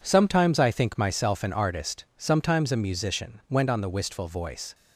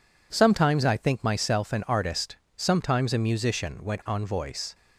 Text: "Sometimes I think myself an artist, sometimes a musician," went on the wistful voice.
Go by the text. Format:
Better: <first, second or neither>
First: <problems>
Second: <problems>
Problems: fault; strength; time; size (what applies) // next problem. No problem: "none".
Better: first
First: none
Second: skips "the wistful"; at 4.2 s